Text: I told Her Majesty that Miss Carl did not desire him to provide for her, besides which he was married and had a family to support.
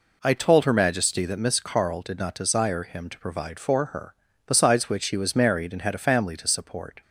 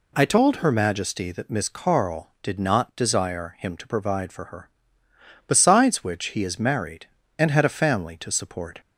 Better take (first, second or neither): first